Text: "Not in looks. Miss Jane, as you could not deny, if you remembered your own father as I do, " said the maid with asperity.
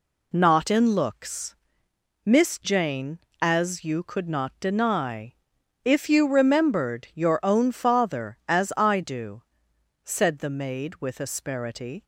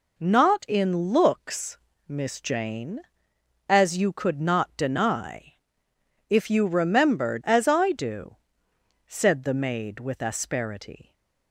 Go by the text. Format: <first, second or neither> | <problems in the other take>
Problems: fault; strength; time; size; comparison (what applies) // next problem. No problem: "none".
first | skips "your own father"; at 7.4 s